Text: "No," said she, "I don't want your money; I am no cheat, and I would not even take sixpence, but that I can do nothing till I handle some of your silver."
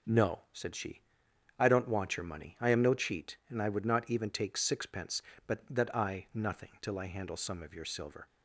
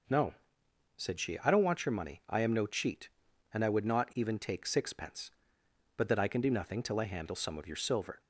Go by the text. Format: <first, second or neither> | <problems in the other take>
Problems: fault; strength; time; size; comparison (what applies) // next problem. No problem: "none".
second | skips "can do"; at 6.2 s